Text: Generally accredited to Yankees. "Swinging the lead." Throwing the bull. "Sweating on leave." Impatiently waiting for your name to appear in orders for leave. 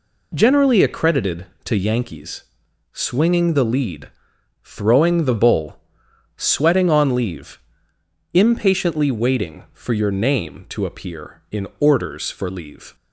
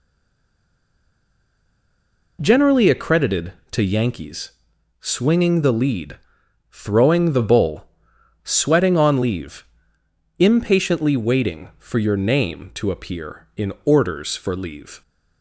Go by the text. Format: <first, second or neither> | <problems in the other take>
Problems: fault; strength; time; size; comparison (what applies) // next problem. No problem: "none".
first | stays silent before the first word; until 2.3 s; 2.3 s long